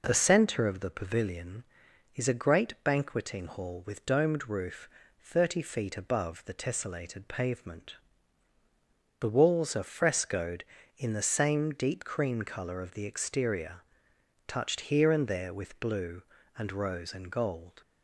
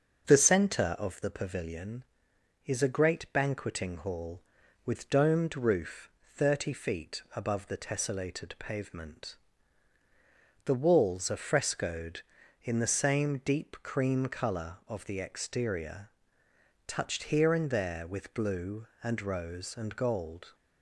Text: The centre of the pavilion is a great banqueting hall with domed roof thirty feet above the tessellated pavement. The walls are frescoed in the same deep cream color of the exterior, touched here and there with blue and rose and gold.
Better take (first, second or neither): first